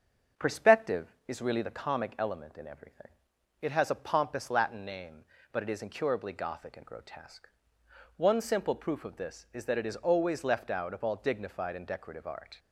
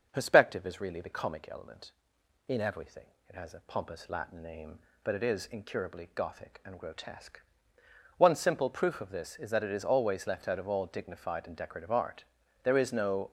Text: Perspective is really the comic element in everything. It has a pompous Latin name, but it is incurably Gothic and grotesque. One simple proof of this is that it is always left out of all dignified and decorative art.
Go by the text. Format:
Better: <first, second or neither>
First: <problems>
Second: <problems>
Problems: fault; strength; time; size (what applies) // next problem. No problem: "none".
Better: first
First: starts louder than the rest; until 1.6 s; 7 dB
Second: starts louder than the rest; noticeable; until 1.1 s; 6 dB // goes on to say "There is no"; noticeable; from 12.6 s on; 0.68 s long